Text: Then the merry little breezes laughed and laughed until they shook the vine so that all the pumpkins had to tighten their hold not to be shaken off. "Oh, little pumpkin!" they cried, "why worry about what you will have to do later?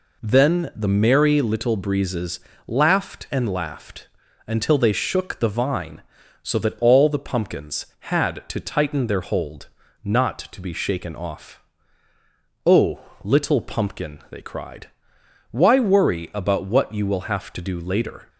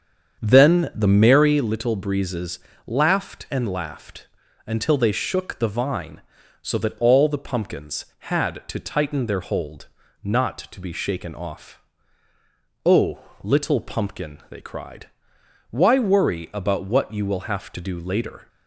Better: first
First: pauses between "breezes" and "laughed"; slight; at 2.3 s; 0.28 s long // pauses between "laughed" and "until"; at 4.0 s; 0.38 s long // pauses between "hold" and "not"; slight; at 9.6 s; 0.34 s long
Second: starts louder than the rest; strong; until 1.6 s; 7.5 dB // pauses between "breezes" and "laughed"; slight; at 2.5 s; 0.28 s long // pauses between "laughed" and "until"; at 4.2 s; 0.38 s long // pauses between "hold" and "not"; slight; at 9.8 s; 0.34 s long

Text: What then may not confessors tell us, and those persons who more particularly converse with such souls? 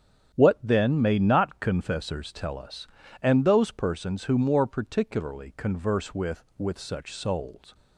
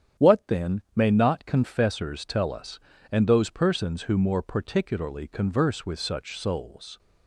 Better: second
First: starts louder than the rest; strong; until 1.3 s; 9 dB // says "with" twice; at 6.5 s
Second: starts louder than the rest; strong; until 1.3 s; 9 dB

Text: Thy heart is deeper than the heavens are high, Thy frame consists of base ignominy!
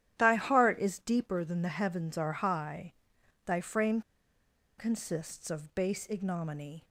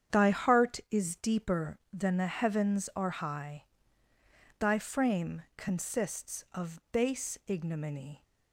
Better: second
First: starts louder than the rest; strong; until 1.1 s; 11 dB // pauses between "frame" and "consists"; noticeable; at 4.0 s; 0.77 s long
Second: starts louder than the rest; strong; until 1.2 s; 8.5 dB

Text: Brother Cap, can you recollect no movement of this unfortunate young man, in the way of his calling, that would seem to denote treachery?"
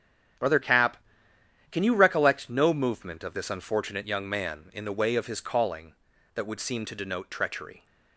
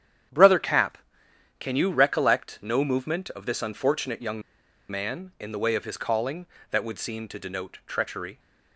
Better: first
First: starts louder than the rest; strong; until 2.1 s; 9.5 dB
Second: starts louder than the rest; strong; until 1.9 s; 9.5 dB // pauses between "young" and "man"; noticeable; at 4.4 s; 0.48 s long

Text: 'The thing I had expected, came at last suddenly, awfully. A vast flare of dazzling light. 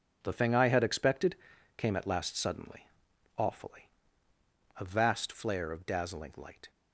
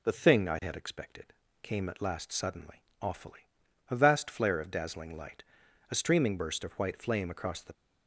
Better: first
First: none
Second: goes on to say "A streaming burst of white flame across the"; strong; from 5.9 s on; 1.8 s long

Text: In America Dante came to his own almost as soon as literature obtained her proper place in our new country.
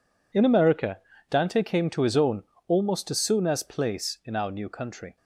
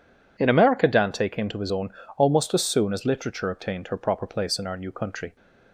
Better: second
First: pauses between "America" and "Dante"; slight; at 0.9 s; 0.30 s long // pauses between "own" and "almost"; slight; at 2.4 s; 0.24 s long // skips "literature obtained her proper"; at 3.6 s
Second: pauses between "own" and "almost"; slight; at 1.9 s; 0.26 s long

